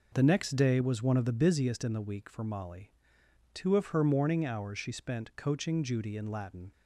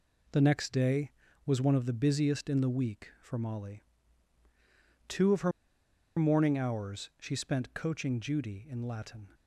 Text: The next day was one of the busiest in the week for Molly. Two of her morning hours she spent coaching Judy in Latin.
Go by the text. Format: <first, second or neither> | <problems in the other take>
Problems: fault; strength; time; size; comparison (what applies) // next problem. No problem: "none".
first | pauses between "her" and "morning"; noticeable; at 5.5 s; 0.67 s long